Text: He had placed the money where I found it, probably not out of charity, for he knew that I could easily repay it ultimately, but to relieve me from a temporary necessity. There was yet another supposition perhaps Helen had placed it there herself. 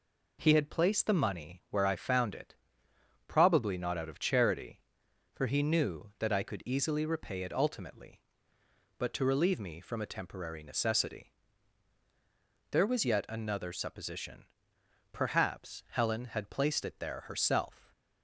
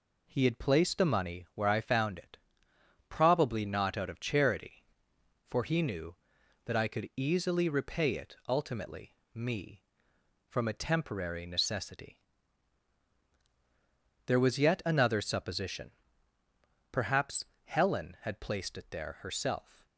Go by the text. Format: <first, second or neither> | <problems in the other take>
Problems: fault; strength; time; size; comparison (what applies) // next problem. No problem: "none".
first | skips "but to relieve"; at 9.2 s // pauses between "supposition" and "perhaps"; at 15.9 s; 1.0 s long; noticeable in the first // pauses between "perhaps" and "Helen"; slight; at 17.4 s; 0.20 s long